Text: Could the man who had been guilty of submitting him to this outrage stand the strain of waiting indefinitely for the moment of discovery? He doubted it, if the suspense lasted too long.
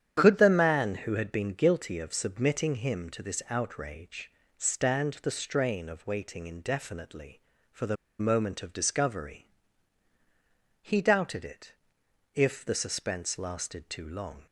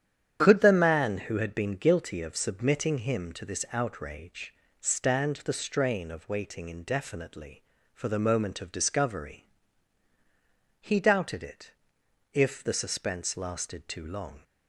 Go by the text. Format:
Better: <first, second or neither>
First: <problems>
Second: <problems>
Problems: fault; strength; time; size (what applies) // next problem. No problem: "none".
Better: second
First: starts louder than the rest; strong; until 1.2 s; 9 dB // pauses between "outrage" and "stand"; slight; at 4.3 s; 0.24 s long // pauses between "the" and "moment"; slight; at 7.9 s; 0.23 s long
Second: starts louder than the rest; strong; until 1.4 s; 9 dB // pauses between "outrage" and "stand"; slight; at 4.5 s; 0.24 s long